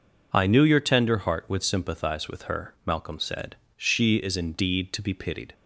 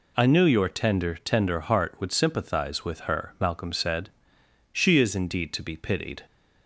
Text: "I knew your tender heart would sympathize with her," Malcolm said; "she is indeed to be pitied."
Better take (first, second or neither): first